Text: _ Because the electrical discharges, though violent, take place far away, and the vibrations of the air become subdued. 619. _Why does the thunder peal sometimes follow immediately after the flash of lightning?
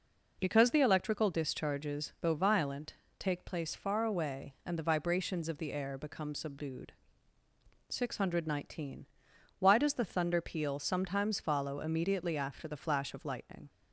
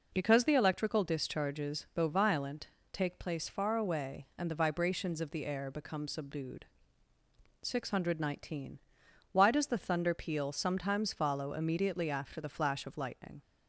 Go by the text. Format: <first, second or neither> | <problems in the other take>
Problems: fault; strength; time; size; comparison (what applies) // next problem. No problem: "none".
neither | none